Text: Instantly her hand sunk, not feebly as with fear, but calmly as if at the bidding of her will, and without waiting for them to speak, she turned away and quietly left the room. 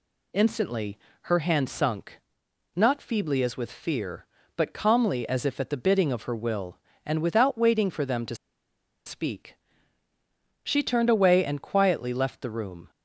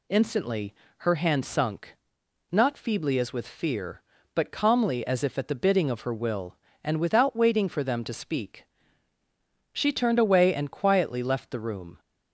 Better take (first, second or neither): second